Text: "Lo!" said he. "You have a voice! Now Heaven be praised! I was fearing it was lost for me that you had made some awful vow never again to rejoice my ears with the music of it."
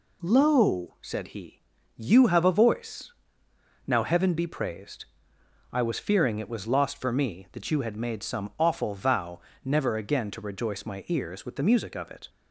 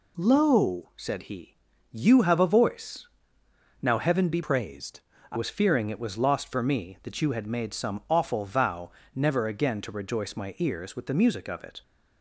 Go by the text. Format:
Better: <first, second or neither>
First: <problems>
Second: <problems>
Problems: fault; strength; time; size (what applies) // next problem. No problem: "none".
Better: first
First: pauses between "vow" and "never"; slight; at 9.3 s; 0.24 s long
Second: changes voice from "praised" to "I"; from 4.4 to 5.3 s; 0.9 s long // pauses between "vow" and "never"; slight; at 8.9 s; 0.24 s long